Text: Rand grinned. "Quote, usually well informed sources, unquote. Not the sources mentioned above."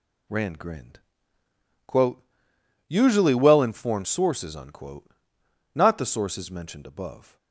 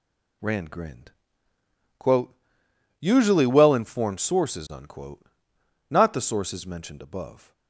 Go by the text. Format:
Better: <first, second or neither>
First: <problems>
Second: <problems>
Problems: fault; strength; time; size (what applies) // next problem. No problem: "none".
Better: neither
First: none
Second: none